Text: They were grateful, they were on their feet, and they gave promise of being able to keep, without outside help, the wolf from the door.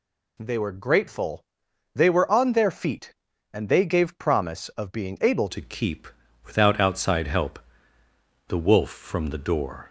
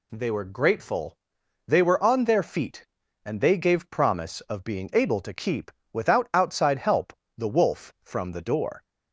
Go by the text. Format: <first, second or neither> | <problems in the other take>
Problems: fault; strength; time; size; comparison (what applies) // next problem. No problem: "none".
second | changes voice at "to"; from 5.4 s on; 4.4 s long